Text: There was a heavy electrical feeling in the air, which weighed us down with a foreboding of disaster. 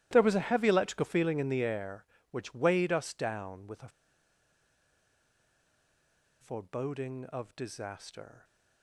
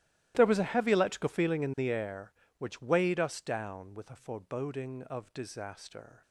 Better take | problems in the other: second | starts louder than the rest; strong; until 1.1 s; 14 dB; strong in the second // pauses between "a" and "foreboding"; strong; at 3.8 s; 2.5 s long

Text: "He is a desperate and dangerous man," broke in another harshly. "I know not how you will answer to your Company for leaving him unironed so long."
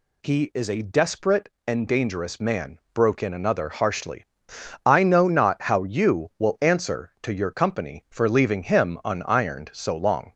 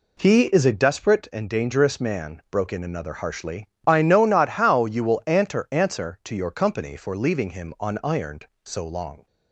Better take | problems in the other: first | says "answer" twice; at 5.7 s

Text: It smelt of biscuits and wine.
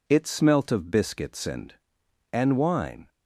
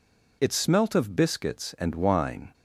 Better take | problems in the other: second | says "and" twice; at 2.3 s

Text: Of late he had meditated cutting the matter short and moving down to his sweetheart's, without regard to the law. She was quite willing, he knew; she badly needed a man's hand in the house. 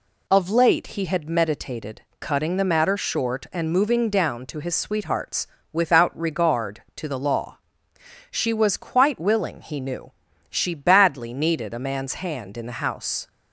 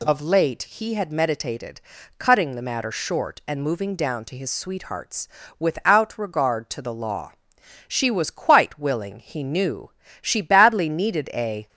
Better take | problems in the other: first | pauses between "meditated" and "cutting"; at 1.8 s; 0.38 s long; slight in the first // stops before "man's hand in the house"; at 11.6 s

